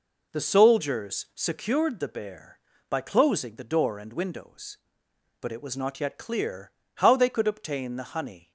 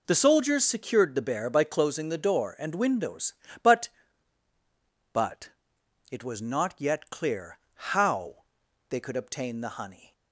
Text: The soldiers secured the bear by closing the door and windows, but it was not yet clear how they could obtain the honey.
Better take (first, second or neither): first